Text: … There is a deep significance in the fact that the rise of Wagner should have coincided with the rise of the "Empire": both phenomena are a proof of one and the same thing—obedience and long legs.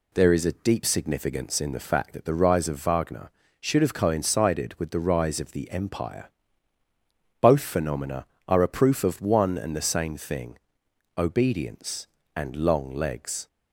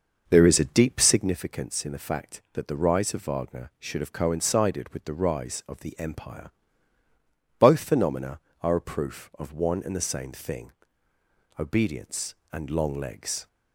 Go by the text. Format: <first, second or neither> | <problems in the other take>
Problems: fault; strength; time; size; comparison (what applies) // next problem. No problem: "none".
first | starts louder than the rest; noticeable; until 1.4 s; 6 dB